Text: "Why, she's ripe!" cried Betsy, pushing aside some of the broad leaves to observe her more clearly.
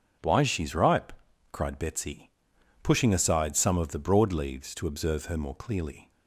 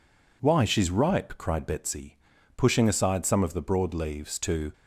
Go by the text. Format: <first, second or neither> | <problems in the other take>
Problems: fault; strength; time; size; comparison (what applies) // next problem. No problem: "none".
first | stops before "observe her more clearly"; at 4.7 s